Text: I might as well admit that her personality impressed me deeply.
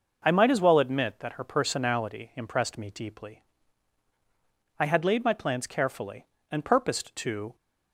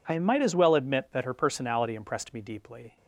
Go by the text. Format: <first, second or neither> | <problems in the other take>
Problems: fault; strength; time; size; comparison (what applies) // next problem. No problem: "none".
second | goes on to say "I had laid my plans carefully and purposed to"; strong; from 4.7 s on; 2.7 s long